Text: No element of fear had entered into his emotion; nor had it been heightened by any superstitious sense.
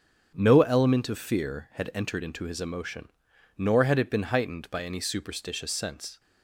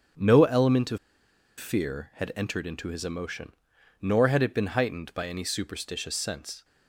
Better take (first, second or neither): first